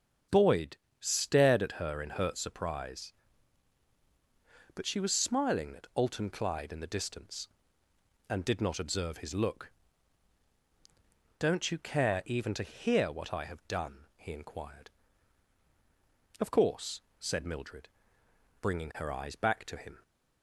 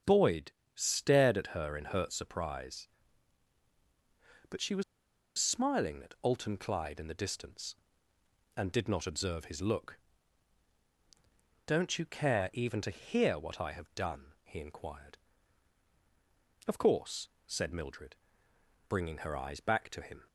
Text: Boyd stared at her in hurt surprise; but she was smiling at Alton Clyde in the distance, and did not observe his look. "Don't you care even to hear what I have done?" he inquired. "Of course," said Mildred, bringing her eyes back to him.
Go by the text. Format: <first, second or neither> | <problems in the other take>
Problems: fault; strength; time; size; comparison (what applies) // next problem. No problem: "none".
first | starts louder than the rest; strong; until 1.2 s; 7.5 dB; strong in the first // pauses between "Boyd" and "stared"; slight; at 0.5 s; 0.22 s long; slight in the first // pauses between "was" and "smiling"; noticeable; at 4.8 s; 0.55 s long